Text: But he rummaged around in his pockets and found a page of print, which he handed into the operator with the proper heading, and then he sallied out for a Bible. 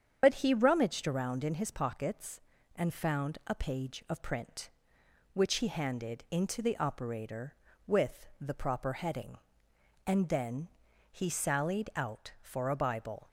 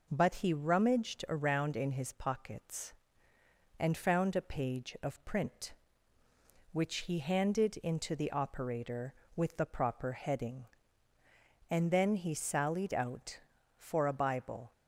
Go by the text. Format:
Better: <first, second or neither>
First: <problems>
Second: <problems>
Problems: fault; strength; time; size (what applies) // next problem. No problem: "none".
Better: second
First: loses the start of "But"; at 0.2 s; 70 ms // starts louder than the rest; strong; until 1.2 s; 7.5 dB // pauses between "then" and "he"; at 10.6 s; 0.42 s long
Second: none